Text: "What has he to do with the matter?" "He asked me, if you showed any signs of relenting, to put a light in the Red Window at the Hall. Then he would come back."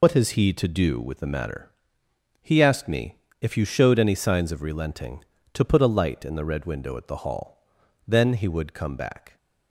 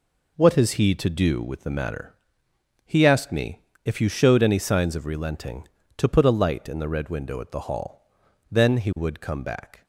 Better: second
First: loses the start of "What"; at 0.0 s; 80 ms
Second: none

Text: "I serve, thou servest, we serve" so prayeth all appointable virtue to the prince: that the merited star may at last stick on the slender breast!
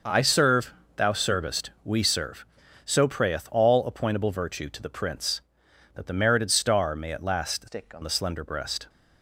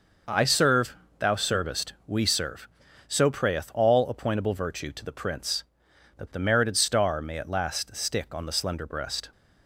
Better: second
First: changes voice from "stick" to "on"; from 7.6 to 8.0 s; 0.4 s long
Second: none

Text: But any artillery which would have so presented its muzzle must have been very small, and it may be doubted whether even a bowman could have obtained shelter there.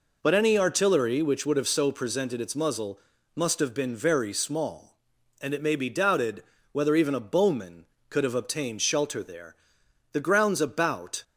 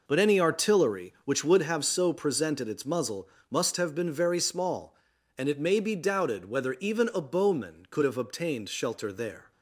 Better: second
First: pauses between "muzzle" and "must"; slight; at 2.9 s; 0.36 s long // pauses between "doubted" and "whether"; slight; at 6.4 s; 0.28 s long // goes on to say "The grounds about"; noticeable; from 10.1 s on; 1.1 s long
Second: pauses between "muzzle" and "must"; slight; at 3.2 s; 0.24 s long

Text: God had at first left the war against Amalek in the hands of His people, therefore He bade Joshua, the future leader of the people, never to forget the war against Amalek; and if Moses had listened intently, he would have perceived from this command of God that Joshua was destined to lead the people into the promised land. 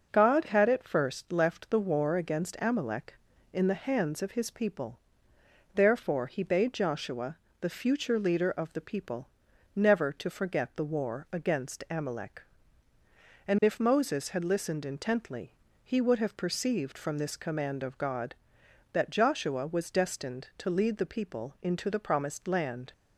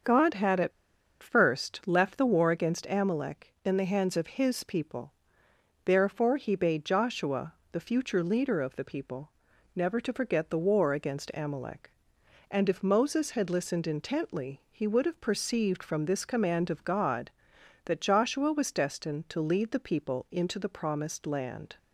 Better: first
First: none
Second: starts louder than the rest; until 1.5 s; 7 dB // pauses between "at" and "first"; noticeable; at 0.7 s; 0.52 s long

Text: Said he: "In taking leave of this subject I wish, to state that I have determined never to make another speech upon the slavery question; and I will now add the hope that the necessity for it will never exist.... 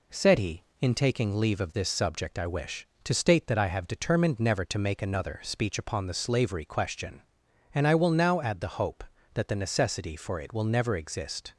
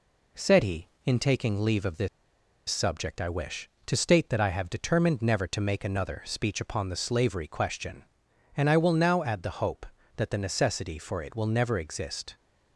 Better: first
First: none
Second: pauses between "this" and "subject"; noticeable; at 2.0 s; 0.60 s long

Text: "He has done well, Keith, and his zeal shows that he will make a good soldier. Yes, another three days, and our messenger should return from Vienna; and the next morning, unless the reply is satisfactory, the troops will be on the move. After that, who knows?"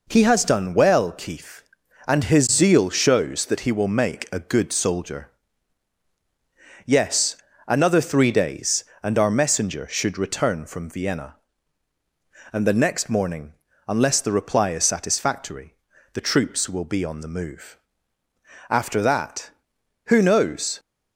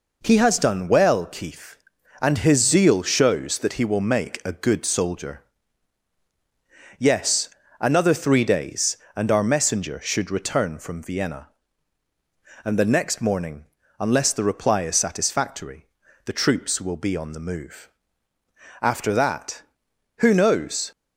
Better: neither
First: none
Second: none

